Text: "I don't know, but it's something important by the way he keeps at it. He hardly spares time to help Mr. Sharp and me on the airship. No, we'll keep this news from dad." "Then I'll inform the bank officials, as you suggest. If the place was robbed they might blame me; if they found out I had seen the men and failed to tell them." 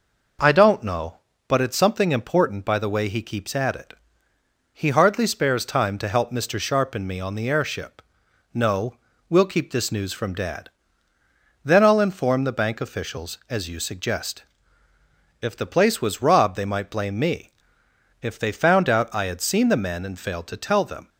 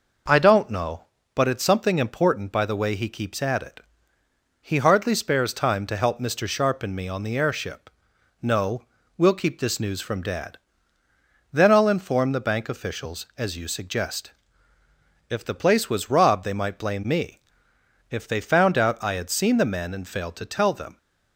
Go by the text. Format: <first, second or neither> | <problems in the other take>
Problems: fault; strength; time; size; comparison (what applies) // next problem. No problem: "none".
neither | none